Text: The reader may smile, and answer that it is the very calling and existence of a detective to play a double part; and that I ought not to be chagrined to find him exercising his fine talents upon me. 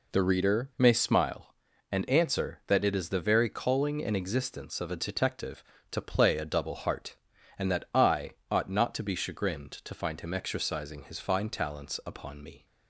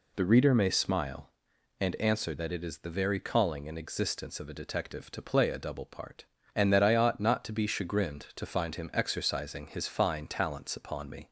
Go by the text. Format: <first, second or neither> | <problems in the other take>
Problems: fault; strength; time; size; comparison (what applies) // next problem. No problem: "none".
second | says "heart" for "part"; at 6.7 s // pauses between "I" and "ought"; slight; at 8.3 s; 0.18 s long